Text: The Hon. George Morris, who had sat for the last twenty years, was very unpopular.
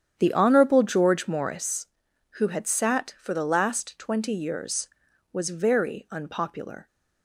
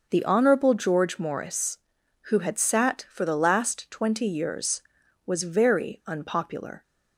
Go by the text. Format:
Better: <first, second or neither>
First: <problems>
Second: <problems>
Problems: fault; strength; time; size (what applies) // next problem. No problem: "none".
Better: second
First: starts louder than the rest; strong; until 1.7 s; 9 dB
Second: none